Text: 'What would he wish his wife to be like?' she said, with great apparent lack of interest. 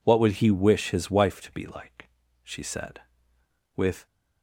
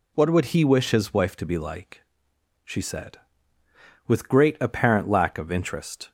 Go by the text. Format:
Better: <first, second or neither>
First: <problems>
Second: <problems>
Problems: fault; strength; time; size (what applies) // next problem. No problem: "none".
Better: second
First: stops before "great apparent lack of interest"; at 4.0 s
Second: none